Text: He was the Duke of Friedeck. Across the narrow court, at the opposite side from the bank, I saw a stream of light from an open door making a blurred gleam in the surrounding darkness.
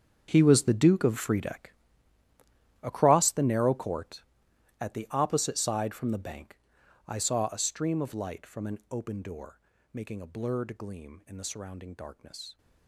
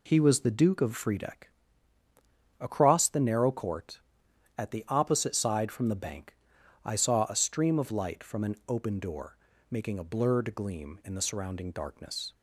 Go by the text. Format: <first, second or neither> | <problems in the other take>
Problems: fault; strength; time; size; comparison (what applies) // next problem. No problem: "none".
second | gets quieter; strong; throughout; 16 dB // pauses between "door" and "making"; slight; at 9.5 s; 0.32 s long; slight in the second